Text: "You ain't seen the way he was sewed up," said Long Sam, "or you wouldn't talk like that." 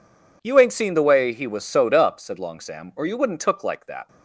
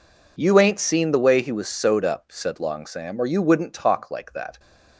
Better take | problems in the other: second | says "took" for "talk"; at 3.4 s

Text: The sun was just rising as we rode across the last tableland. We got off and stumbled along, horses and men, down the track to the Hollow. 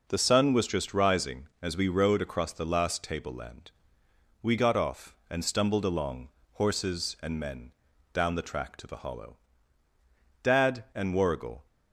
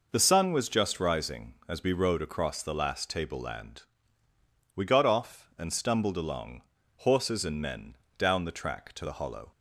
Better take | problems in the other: second | goes on to say "Dad and Warrigal"; noticeable; from 10.4 s on; 1.2 s long

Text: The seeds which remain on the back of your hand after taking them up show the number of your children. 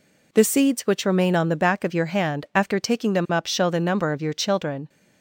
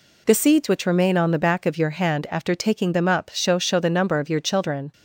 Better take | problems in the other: first | says "show" twice; at 3.5 s

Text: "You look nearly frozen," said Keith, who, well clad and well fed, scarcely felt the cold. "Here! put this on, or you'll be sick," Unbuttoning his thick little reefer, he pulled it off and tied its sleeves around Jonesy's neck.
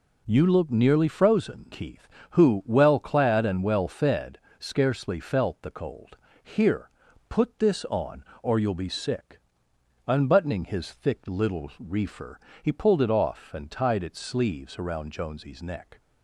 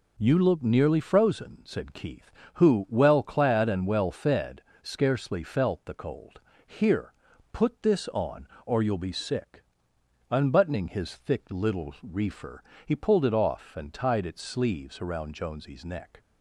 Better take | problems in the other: second | skips "said"; at 1.6 s

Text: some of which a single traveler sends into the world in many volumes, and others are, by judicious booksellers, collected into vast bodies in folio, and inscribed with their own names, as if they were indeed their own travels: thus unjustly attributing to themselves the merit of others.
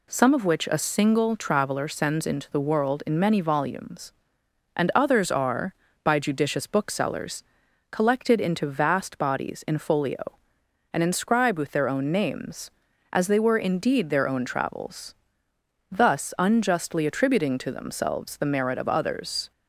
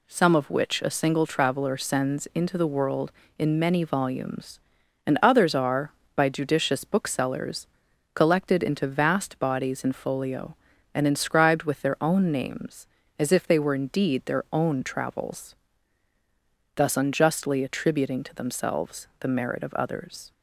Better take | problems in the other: second | skips "if"; at 13.2 s

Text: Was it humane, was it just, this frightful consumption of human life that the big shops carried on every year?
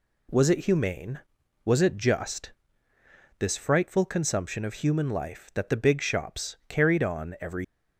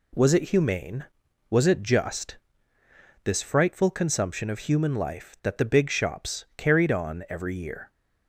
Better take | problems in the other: second | stops before "year"; at 7.6 s

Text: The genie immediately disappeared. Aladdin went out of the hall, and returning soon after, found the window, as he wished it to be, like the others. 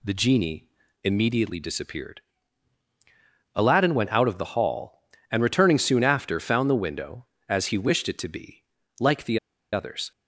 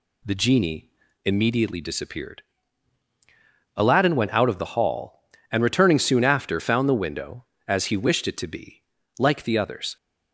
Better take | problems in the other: second | pauses between "genie" and "immediately"; slight; at 0.6 s; 0.36 s long; slight in the second // pauses between "the" and "others"; slight; at 9.3 s; 0.34 s long

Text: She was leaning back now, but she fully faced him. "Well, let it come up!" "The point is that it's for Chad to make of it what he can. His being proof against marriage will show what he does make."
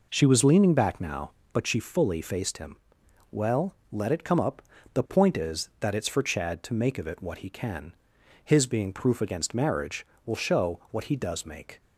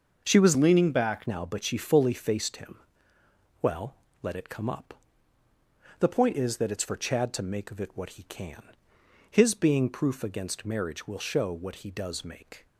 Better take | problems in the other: first | starts louder than the rest; noticeable; until 1.2 s; 6 dB // changes voice from "leaning" to "back"; from 0.5 to 1.2 s; 0.7 s long

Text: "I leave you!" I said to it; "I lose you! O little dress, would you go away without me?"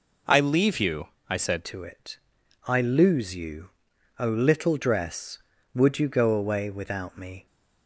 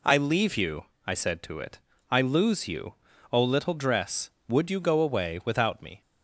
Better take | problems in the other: second | changes voice at "to"; from 1.6 s on; 5.8 s long

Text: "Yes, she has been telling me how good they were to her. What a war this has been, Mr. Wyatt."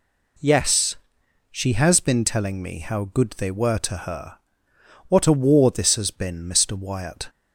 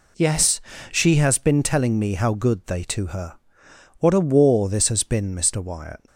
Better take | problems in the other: first | skips "were"; at 2.8 s

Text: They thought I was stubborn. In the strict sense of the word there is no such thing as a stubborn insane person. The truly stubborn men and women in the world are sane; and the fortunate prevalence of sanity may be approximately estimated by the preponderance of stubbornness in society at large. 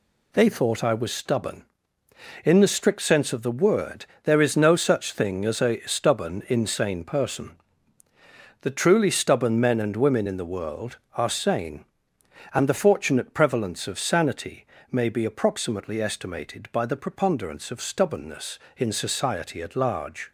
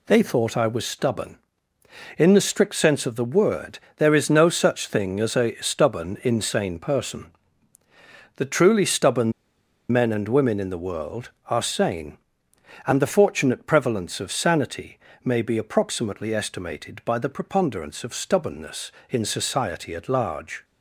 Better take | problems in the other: first | pauses between "word" and "there"; slight; at 3.7 s; 0.18 s long; slight in the first // pauses between "stubborn" and "men"; noticeable; at 9.3 s; 0.59 s long // pauses between "sanity" and "may"; slight; at 14.9 s; 0.26 s long; slight in the first

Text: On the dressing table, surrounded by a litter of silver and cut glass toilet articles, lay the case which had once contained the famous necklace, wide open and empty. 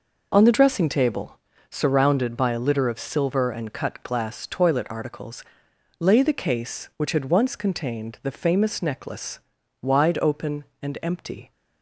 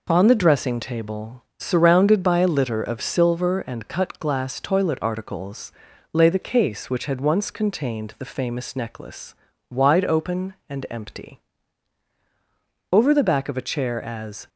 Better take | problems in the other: first | goes on to say "Over the back of a chair as"; from 12.9 s on; 1.5 s long

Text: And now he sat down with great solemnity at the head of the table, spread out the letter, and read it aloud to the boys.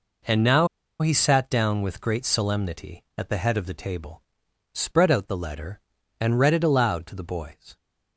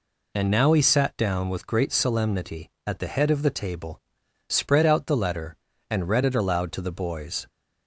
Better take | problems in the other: second | pauses between "now" and "he"; slight; at 0.6 s; 0.34 s long

